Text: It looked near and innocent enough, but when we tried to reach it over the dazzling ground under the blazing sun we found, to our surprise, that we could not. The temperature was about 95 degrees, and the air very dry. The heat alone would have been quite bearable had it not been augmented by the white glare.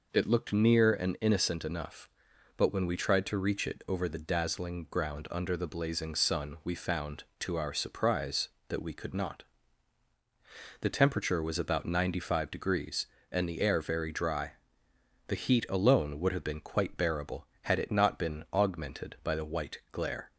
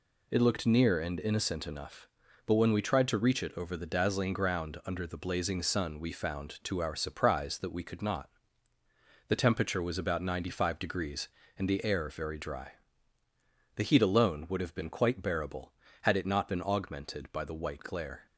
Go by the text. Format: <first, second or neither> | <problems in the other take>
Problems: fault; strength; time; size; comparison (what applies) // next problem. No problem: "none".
neither | none